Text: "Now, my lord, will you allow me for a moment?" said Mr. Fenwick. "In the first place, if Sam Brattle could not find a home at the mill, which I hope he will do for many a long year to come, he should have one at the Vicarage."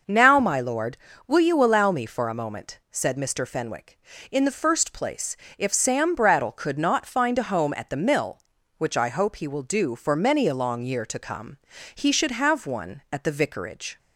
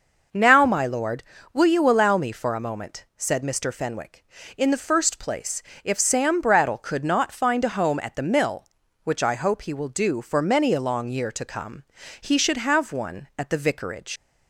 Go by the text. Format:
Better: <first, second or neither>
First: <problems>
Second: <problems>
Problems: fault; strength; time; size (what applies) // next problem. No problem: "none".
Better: first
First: none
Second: leaves "Vicarage" unfinished; at 14.1 s; 80 ms